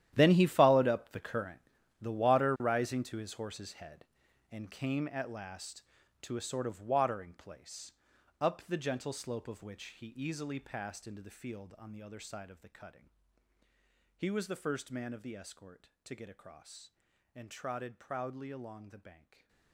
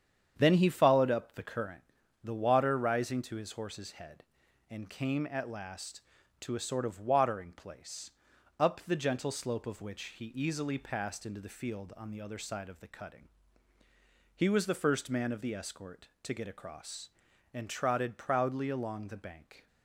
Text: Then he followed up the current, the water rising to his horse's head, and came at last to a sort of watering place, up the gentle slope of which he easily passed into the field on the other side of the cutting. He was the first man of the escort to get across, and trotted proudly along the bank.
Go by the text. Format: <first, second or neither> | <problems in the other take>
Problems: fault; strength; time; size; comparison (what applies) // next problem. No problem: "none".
second | gets quieter; strong; throughout; 16.5 dB // starts louder than the rest; strong; until 1.1 s; 11.5 dB; strong in the second // stays silent after the last word; slight; from 19.1 s on; 0.6 s long